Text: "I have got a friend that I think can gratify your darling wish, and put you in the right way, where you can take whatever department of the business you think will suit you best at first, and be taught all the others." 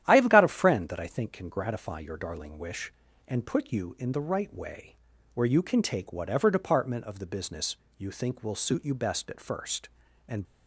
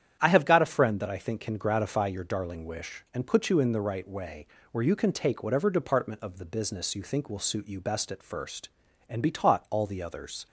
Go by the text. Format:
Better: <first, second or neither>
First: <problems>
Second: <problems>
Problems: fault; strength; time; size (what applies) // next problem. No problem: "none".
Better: second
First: starts louder than the rest; strong; until 1.0 s; 11 dB // pauses between "business" and "you"; slight; at 7.7 s; 0.22 s long // stops before "be taught all the others"; at 10.4 s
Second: starts louder than the rest; strong; until 1.2 s; 9 dB